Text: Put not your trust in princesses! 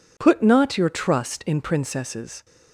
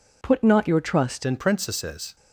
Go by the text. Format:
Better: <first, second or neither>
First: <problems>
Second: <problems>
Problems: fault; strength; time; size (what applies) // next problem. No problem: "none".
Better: first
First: none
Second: changes voice at "in"; from 1.2 s on; 0.9 s long